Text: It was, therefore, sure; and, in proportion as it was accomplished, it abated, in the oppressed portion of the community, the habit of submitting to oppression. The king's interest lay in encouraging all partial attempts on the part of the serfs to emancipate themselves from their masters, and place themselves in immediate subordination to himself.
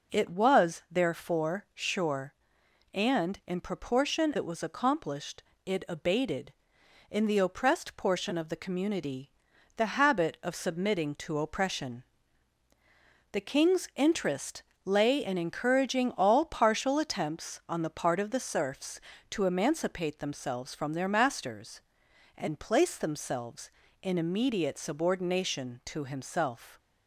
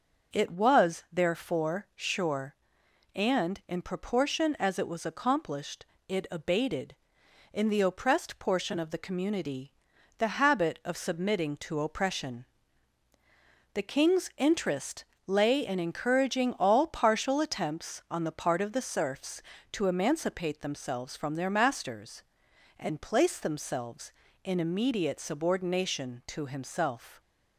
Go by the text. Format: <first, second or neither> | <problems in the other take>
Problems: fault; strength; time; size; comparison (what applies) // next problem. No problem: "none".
second | skips "as"; at 4.3 s // pauses between "interest" and "lay"; slight; at 14.6 s; 0.22 s long; slight in the second